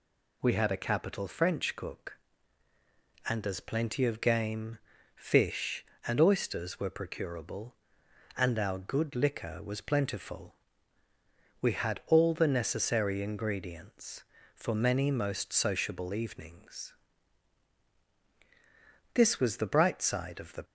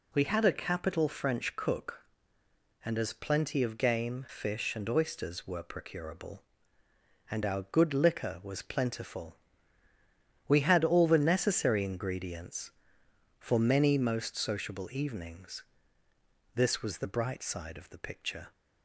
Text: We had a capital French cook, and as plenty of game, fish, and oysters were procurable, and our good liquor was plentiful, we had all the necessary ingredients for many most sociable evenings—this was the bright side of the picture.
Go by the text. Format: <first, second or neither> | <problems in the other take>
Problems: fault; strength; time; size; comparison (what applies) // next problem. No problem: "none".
second | stops before "picture"; at 20.6 s